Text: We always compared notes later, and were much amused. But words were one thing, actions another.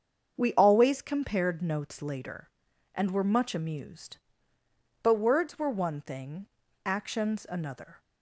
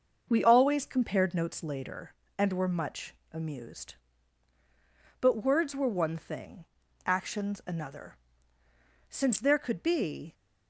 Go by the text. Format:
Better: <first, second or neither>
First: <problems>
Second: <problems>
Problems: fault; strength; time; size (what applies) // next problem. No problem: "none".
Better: first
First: starts louder than the rest; until 1.4 s; 7 dB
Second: starts louder than the rest; until 1.3 s; 6 dB // pauses between "much" and "amused"; slight; at 3.1 s; 0.18 s long // goes on to say "Since there could be"; noticeable; from 9.1 s on; 1.1 s long